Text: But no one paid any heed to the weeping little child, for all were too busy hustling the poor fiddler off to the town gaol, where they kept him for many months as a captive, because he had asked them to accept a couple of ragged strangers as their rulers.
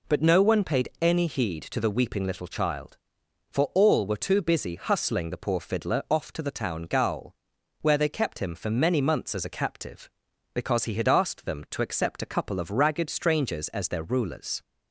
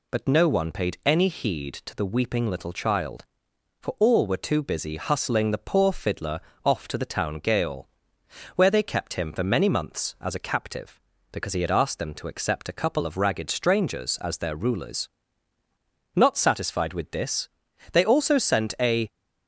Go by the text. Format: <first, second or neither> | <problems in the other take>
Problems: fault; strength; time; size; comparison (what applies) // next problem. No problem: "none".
first | pauses between "fiddler" and "off"; slight; at 6.3 s; 0.26 s long // goes on to say "Not satisfied with this they also sent a"; strong; from 16.1 s on; 2.9 s long